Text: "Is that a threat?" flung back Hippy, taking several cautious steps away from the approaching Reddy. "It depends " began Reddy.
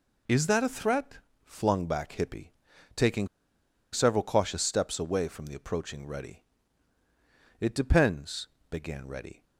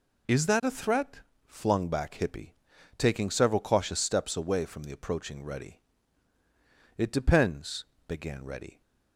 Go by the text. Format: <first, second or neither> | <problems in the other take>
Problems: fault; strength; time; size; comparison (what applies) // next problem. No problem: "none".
second | pauses between "taking" and "several"; noticeable; at 3.2 s; 0.64 s long